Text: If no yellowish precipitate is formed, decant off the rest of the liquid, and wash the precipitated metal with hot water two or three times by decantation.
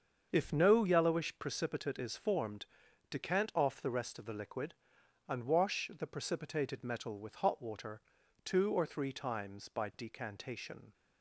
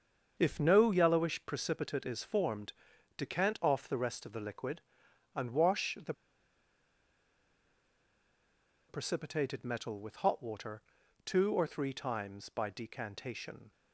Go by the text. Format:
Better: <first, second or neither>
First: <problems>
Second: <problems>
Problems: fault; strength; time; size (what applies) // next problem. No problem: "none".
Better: first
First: starts louder than the rest; until 1.3 s; 7 dB // pauses between "water" and "two"; at 8.0 s; 0.44 s long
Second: starts louder than the rest; until 1.4 s; 7 dB // pauses between "the" and "precipitated"; strong; at 6.1 s; 2.7 s long // pauses between "water" and "two"; at 10.8 s; 0.44 s long